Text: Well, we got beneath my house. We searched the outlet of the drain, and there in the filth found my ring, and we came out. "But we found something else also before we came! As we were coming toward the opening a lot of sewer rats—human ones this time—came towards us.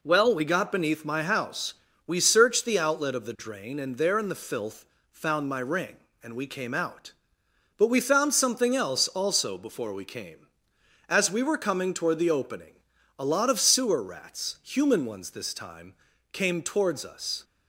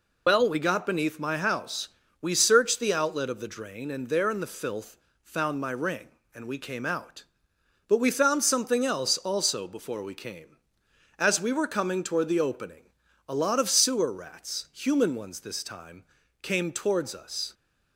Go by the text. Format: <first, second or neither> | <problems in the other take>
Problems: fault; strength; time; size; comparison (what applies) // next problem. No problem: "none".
first | loses the start of "Well"; at 0.2 s; 95 ms // pauses between "filth" and "found"; slight; at 4.9 s; 0.28 s long; slight in the first // pauses between "opening" and "a"; at 12.8 s; 0.44 s long; also in the first